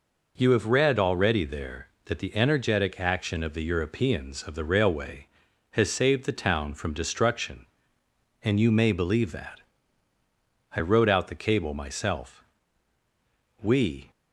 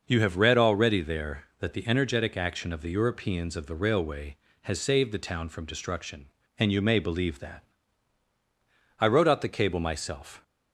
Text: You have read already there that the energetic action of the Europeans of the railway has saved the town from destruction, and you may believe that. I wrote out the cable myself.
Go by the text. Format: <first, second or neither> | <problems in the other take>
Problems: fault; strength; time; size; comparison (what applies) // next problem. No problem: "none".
second | goes on to say "We"; slight; from 13.6 s on; 0.48 s long